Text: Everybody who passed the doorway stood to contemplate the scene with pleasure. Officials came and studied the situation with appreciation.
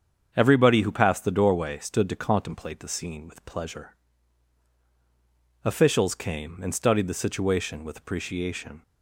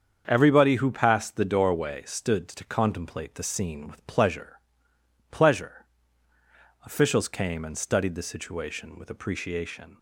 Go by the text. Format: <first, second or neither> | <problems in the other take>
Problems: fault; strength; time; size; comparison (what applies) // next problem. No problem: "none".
first | starts louder than the rest; strong; until 1.2 s; 7.5 dB; strong in the first // says "pleasure" twice; at 5.2 s